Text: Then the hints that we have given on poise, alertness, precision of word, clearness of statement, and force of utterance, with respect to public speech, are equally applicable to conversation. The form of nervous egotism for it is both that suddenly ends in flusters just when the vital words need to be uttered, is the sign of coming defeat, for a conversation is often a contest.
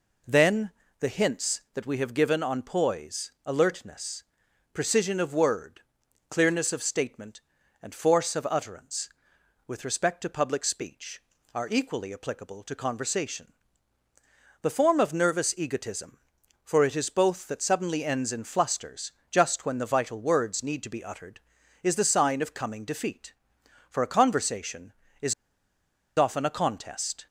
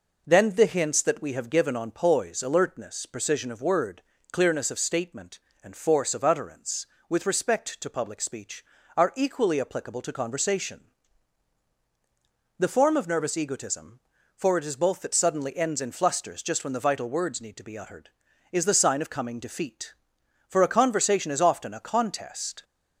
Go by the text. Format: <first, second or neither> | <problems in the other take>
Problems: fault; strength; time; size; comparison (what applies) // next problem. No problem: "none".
second | pauses between "Then" and "the"; slight; at 0.7 s; 0.28 s long // pauses between "flusters" and "just"; slight; at 19.1 s; 0.18 s long // pauses between "is" and "often"; noticeable; at 25.3 s; 0.84 s long